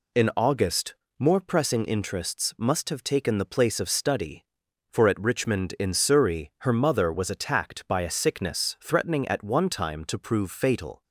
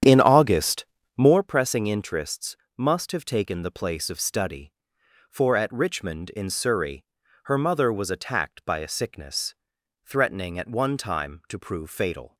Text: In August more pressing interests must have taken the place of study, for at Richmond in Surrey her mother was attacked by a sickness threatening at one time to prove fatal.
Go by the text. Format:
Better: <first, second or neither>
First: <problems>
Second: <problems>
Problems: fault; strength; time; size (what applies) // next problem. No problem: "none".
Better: first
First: pauses between "August" and "more"; slight; at 0.9 s; 0.24 s long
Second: starts louder than the rest; strong; until 1.4 s; 9.5 dB // pauses between "August" and "more"; slight; at 0.8 s; 0.32 s long // pauses between "interests" and "must"; slight; at 2.5 s; 0.18 s long // pauses between "Surrey" and "her"; at 7.0 s; 0.40 s long // pauses between "sickness" and "threatening"; noticeable; at 9.5 s; 0.50 s long